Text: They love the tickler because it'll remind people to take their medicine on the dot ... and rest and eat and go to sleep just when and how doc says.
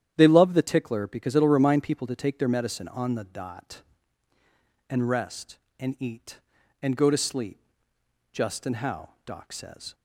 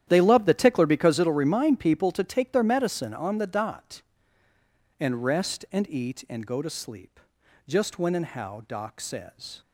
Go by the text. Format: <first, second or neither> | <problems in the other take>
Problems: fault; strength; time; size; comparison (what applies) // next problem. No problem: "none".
second | starts louder than the rest; strong; until 1.1 s; 10 dB; strong in the second // pauses between "sleep" and "just"; noticeable; at 7.5 s; 0.74 s long; noticeable in the second // skips "when"; at 8.6 s // pauses between "how" and "doc"; slight; at 9.1 s; 0.16 s long